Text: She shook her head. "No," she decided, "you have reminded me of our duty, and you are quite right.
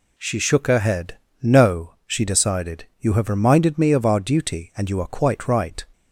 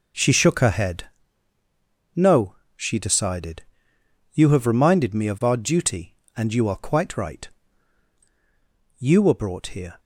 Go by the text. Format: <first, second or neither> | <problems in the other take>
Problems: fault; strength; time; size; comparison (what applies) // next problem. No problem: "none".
first | goes on to say "You were brought here"; noticeable; from 8.9 s on; 1.0 s long